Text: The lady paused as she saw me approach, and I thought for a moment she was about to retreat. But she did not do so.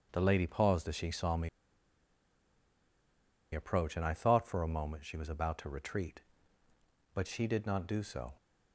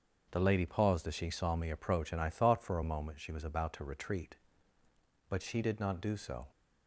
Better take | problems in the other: second | starts louder than the rest; until 1.1 s; 6.5 dB; also in the second // pauses between "me" and "approach"; strong; at 1.4 s; 2.0 s long

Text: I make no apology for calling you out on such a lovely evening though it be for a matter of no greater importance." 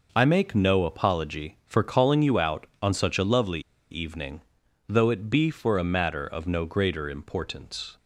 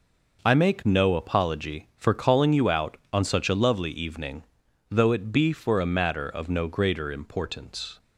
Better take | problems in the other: second | pauses between "lovely" and "evening"; slight; at 3.6 s; 0.30 s long // pauses between "evening" and "though"; noticeable; at 4.3 s; 0.48 s long; noticeable in the second

